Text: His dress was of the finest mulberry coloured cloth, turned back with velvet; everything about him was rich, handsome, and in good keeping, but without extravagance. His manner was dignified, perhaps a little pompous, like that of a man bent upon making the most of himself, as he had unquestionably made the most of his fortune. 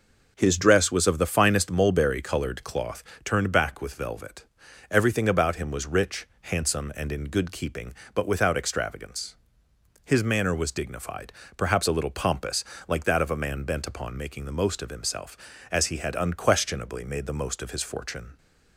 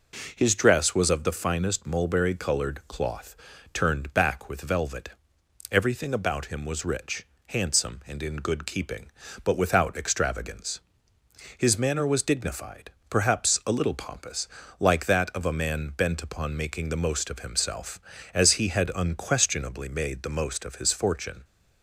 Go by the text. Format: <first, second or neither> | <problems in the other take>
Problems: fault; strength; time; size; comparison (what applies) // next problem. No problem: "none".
neither | none